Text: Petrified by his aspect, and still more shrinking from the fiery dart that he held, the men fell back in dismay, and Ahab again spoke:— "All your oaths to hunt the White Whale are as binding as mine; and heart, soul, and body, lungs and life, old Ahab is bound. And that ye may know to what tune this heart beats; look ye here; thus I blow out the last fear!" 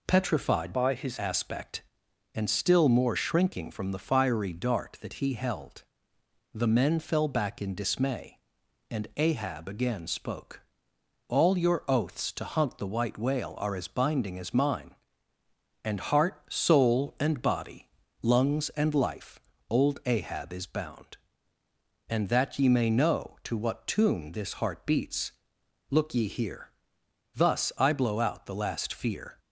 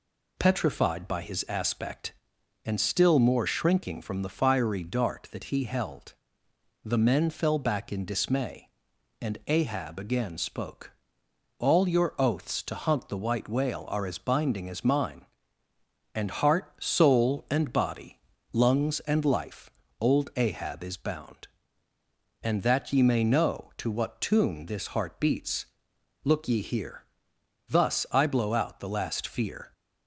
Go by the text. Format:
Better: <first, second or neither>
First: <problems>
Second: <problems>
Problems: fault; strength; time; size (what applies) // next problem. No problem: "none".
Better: second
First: changes voice from "by" to "his"; from 0.7 to 1.1 s; 0.4 s long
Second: none